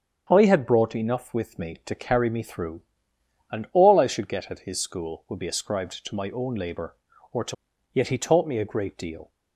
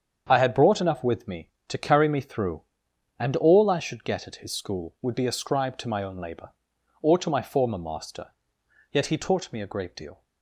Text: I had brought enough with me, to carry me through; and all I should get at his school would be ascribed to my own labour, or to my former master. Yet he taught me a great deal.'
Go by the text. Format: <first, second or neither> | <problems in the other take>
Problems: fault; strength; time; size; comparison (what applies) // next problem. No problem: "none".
second | starts louder than the rest; strong; until 1.3 s; 8 dB; strong in the second // skips "my former master"; at 7.7 s